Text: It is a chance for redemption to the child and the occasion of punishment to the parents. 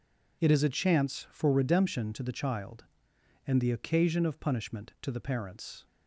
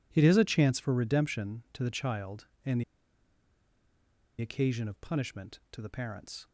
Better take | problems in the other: first | pauses between "and" and "the"; strong; at 2.8 s; 1.5 s long

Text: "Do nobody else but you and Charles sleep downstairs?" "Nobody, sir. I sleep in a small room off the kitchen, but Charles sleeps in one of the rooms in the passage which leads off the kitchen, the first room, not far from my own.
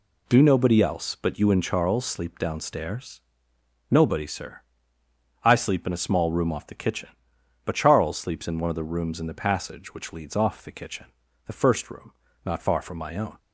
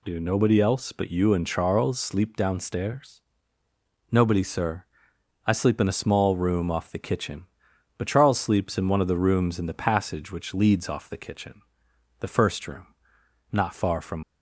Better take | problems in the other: first | stops before "my own"; at 14.2 s

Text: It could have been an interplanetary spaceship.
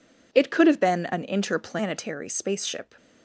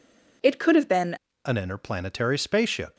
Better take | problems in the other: first | changes voice at "an"; from 1.4 s on; 1.5 s long

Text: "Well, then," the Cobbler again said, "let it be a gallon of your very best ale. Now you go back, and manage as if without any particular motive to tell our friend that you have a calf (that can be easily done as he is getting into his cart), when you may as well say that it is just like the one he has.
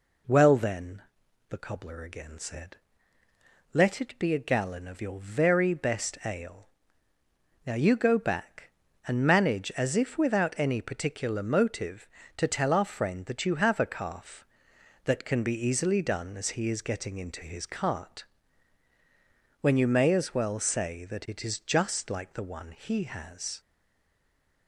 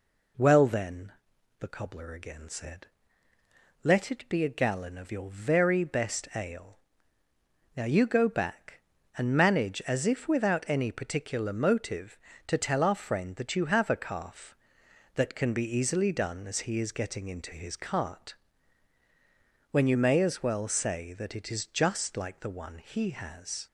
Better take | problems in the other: second | stays silent after the last word; from 23.6 s on; 1.0 s long

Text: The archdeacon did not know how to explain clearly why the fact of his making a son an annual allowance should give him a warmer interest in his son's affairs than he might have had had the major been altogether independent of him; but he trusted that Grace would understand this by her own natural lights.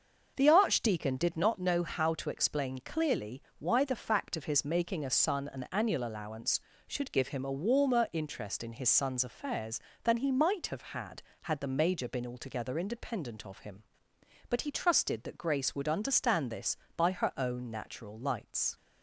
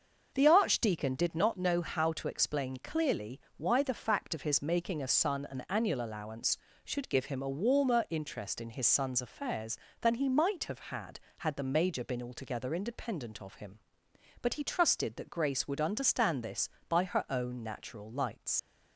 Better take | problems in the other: first | starts louder than the rest; until 1.3 s; 6 dB; also in the first // pauses between "clearly" and "why"; slight; at 3.4 s; 0.16 s long; slight in the first // leaves "lights" unfinished; at 18.5 s; 80 ms

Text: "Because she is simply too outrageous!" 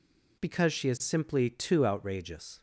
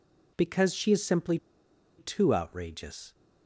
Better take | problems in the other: first | pauses between "simply" and "too"; noticeable; at 1.3 s; 0.61 s long

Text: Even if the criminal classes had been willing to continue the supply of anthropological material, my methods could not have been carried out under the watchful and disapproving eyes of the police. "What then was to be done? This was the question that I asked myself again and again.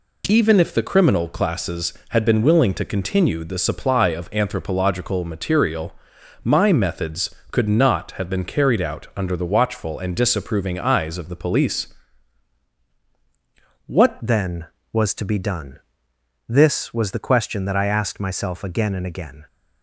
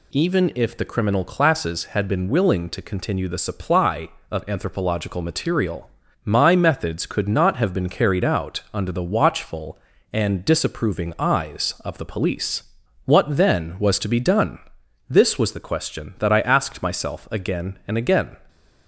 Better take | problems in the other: second | changes voice at "then"; from 14.2 s on; 5.2 s long

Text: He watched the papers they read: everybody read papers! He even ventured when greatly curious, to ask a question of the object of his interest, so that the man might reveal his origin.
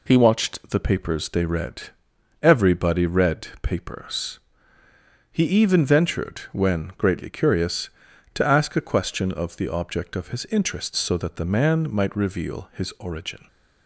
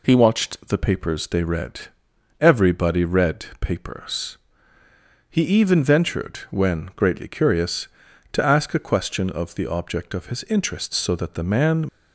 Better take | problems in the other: first | stops before "might reveal his origin"; at 11.8 s

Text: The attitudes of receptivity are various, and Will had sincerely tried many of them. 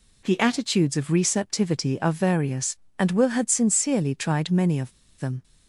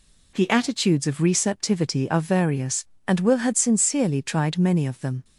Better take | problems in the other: second | pauses between "of" and "them"; slight; at 4.9 s; 0.27 s long

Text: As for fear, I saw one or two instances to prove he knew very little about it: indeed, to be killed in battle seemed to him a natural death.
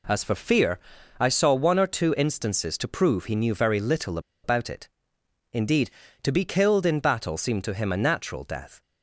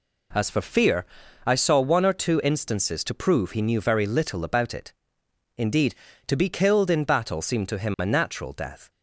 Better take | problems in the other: second | pauses between "little" and "about"; slight; at 4.1 s; 0.24 s long

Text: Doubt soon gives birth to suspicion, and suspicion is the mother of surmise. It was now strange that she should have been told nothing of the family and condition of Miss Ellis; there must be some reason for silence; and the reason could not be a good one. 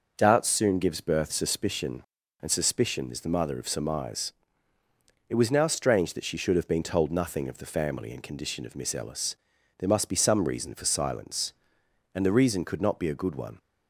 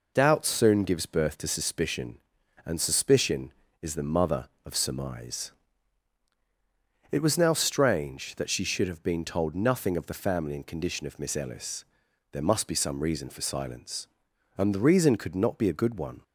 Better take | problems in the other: second | skips "to"; at 1.3 s

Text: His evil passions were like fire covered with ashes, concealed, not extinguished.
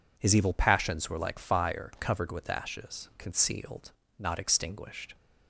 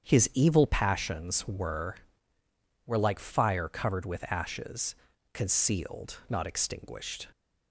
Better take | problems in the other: first | starts louder than the rest; strong; until 1.1 s; 8.5 dB // says "were" twice; at 2.8 s

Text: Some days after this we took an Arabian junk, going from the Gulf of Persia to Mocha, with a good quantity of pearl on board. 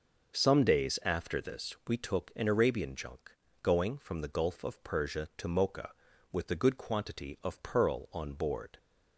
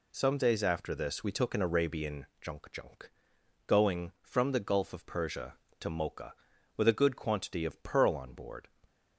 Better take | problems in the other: first | says "junk" twice; at 2.7 s

